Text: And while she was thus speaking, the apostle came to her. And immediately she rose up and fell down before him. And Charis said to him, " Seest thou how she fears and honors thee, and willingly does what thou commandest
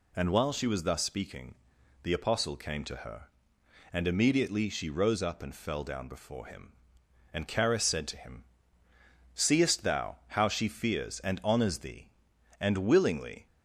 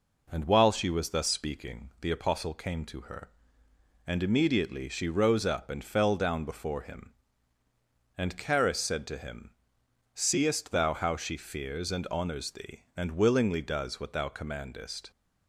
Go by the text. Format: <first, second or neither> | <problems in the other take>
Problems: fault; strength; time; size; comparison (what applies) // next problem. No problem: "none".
second | stops before "does what thou commandest"; at 13.4 s